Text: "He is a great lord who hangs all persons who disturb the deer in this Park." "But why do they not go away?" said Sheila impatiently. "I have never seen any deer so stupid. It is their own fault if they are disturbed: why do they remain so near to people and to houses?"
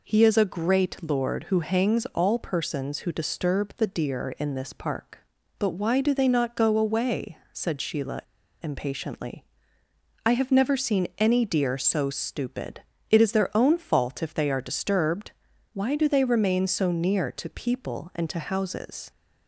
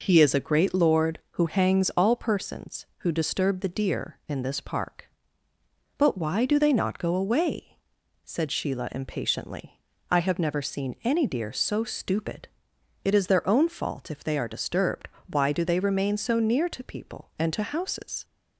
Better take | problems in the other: second | pauses between "Sheila" and "impatiently"; at 8.2 s; 0.42 s long

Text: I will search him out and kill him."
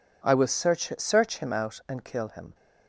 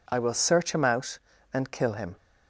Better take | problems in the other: second | says "search" twice; at 0.9 s

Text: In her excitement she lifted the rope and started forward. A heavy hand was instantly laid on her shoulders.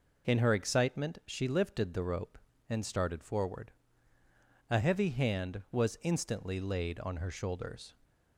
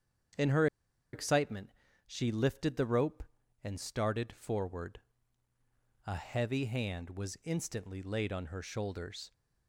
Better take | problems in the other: first | starts louder than the rest; strong; until 2.1 s; 8 dB // pauses between "her" and "excitement"; noticeable; at 0.6 s; 0.47 s long // pauses between "excitement" and "she"; slight; at 1.7 s; 0.36 s long

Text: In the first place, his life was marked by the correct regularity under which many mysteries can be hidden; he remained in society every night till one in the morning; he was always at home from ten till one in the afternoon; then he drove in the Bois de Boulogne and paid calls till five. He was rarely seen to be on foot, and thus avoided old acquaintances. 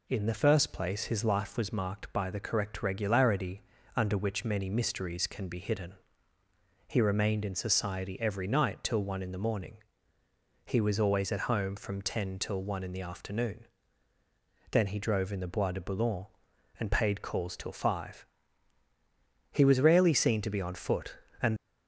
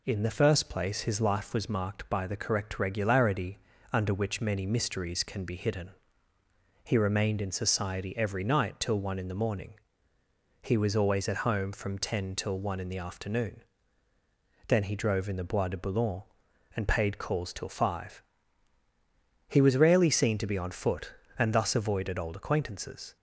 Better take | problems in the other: second | pauses between "regularity" and "under"; slight; at 3.6 s; 0.34 s long; slight in the second // stops before "thus avoided old acquaintances"; at 21.5 s

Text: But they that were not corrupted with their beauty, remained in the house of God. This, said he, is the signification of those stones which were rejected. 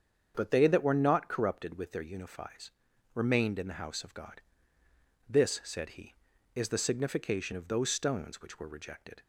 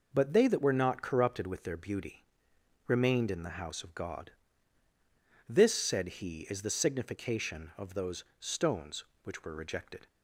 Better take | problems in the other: second | starts louder than the rest; strong; until 1.3 s; 7.5 dB // says "unifies" for "beauty"; at 2.0 s

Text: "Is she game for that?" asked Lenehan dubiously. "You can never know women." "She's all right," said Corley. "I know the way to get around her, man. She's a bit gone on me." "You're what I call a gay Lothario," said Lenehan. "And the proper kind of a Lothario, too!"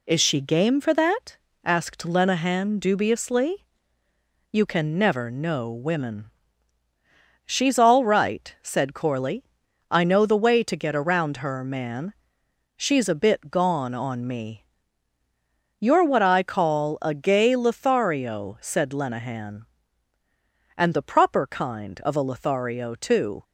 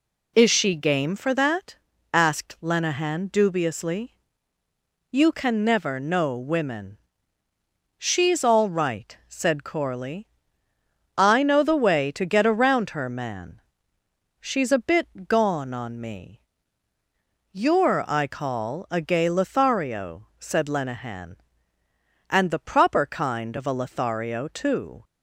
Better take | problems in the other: first | skips "what"; at 18.0 s

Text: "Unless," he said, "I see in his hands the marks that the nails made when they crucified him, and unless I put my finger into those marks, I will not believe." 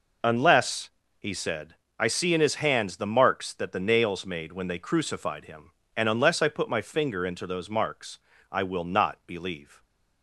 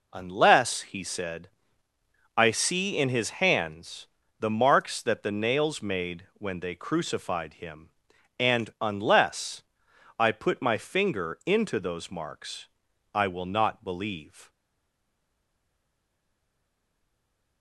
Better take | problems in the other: first | pauses between "hands" and "the"; slight; at 4.0 s; 0.32 s long // pauses between "unless" and "I"; noticeable; at 9.6 s; 0.56 s long // stays silent after the last word; strong; from 14.4 s on; 3.2 s long

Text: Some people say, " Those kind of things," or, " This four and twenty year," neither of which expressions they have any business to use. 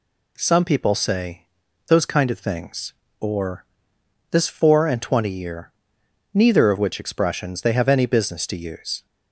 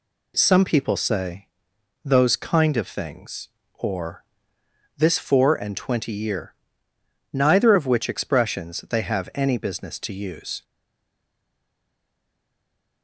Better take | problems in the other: first | stays silent after the last word; from 10.6 s on; 2.4 s long

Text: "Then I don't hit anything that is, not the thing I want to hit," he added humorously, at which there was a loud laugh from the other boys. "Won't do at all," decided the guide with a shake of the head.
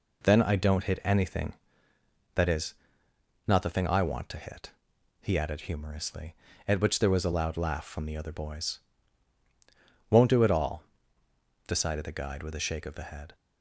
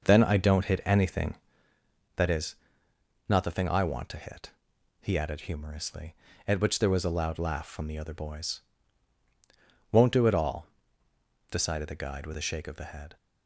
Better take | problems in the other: first | starts louder than the rest; noticeable; until 1.7 s; 5.5 dB

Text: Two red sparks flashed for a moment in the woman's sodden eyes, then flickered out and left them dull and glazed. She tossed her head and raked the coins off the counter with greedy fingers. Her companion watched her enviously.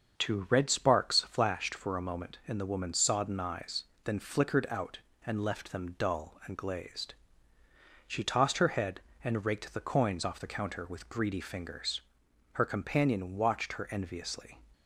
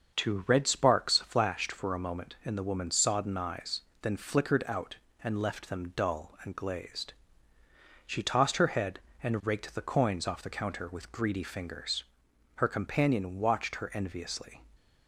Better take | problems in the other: neither | starts louder than the rest; the same in both

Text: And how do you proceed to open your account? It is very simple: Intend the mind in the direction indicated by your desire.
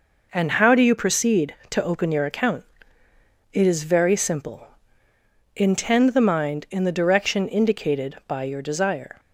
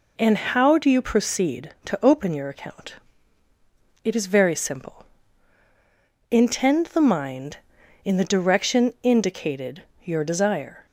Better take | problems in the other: first | skips "by"; at 9.9 s

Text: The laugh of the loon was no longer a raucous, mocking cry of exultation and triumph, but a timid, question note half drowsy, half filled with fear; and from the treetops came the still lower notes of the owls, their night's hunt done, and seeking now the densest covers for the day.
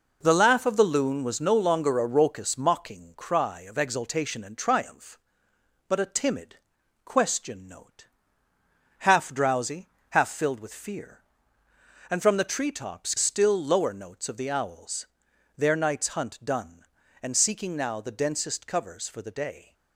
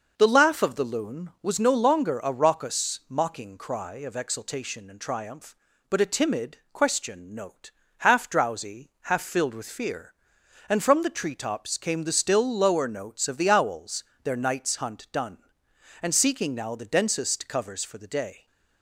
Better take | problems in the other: second | pauses between "note" and "half"; noticeable; at 8.0 s; 0.94 s long; slight in the second // skips "came the"; at 13.1 s

